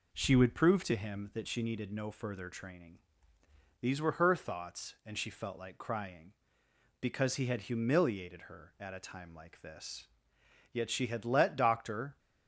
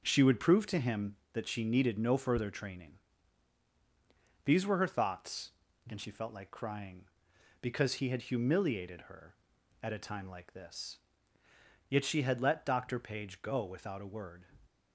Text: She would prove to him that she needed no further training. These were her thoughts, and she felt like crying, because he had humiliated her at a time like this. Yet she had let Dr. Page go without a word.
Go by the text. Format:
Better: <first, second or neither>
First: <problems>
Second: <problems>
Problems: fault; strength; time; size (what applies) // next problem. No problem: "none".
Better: second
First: stops before "Page go without a word"; at 12.1 s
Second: none